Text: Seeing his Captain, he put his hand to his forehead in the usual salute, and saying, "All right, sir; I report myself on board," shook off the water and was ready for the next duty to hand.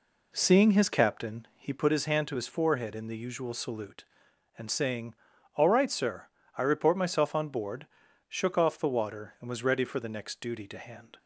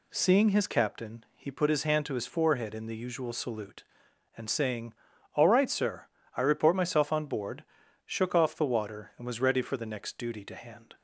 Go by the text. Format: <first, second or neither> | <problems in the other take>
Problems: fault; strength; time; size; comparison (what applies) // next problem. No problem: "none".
second | starts louder than the rest; slight; until 2.0 s; 3 dB